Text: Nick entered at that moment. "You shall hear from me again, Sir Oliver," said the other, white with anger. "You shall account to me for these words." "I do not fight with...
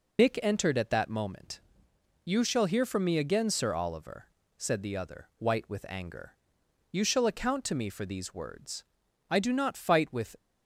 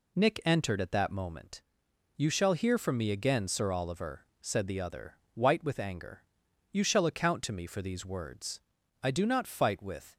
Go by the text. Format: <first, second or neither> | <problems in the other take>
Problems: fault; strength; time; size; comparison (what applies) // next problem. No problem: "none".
second | loses the start of "Nick"; at 0.1 s; 65 ms